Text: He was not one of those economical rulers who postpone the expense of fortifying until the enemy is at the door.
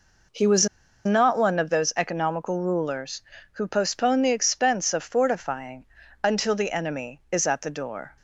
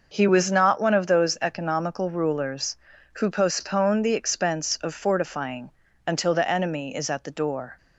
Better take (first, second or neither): second